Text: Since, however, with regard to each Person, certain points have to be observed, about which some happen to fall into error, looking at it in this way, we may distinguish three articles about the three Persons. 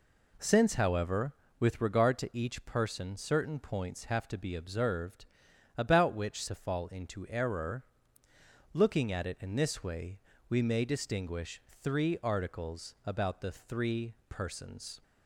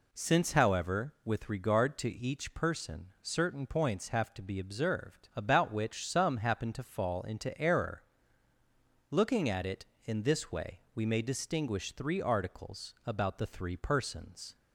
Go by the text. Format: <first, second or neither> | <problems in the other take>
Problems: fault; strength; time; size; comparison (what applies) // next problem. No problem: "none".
second | skips "some happen"; at 6.4 s // pauses between "distinguish" and "three"; slight; at 11.6 s; 0.20 s long // pauses between "three" and "Persons"; slight; at 14.1 s; 0.16 s long